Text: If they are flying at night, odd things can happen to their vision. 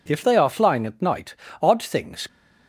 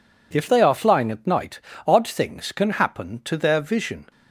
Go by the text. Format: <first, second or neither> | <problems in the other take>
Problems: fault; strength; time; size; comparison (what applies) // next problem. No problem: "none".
second | stops before "can happen to their vision"; at 2.2 s